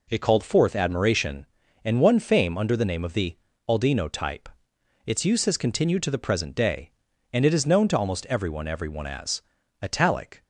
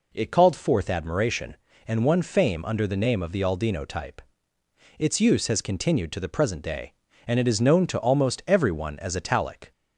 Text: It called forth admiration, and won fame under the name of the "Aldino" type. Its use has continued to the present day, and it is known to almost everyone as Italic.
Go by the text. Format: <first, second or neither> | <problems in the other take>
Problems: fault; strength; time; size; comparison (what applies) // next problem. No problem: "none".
second | pauses between "the" and "Aldino"; slight; at 3.3 s; 0.32 s long // says "everyone" twice; at 8.6 s // pauses between "as" and "Italic"; at 9.4 s; 0.40 s long